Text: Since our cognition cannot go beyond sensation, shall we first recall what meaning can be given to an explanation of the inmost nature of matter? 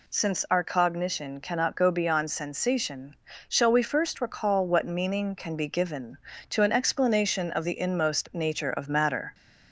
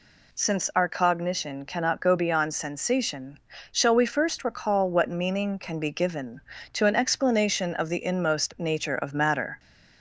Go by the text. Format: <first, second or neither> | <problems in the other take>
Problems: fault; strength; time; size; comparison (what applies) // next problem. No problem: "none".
neither | none